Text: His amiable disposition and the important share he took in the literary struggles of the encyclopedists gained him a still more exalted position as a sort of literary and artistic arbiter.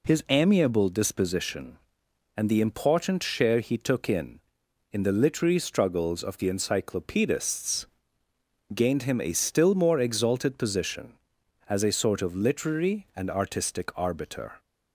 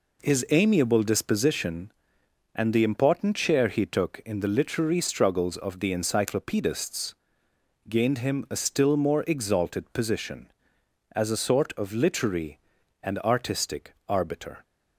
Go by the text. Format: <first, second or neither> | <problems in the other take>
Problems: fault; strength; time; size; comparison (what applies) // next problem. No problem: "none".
second | says "in" twice; at 4.9 s // pauses between "encyclopedists" and "gained"; noticeable; at 7.8 s; 0.84 s long; noticeable in the second